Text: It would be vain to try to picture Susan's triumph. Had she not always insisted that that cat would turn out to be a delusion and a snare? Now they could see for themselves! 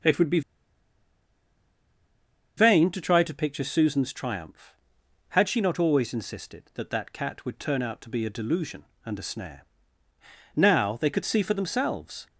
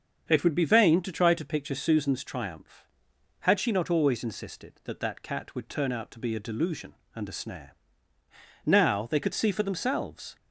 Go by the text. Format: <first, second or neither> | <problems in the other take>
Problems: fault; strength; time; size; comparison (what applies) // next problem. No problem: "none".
second | starts louder than the rest; until 3.2 s; 7 dB; also in the second // pauses between "be" and "vain"; strong; at 0.4 s; 2.1 s long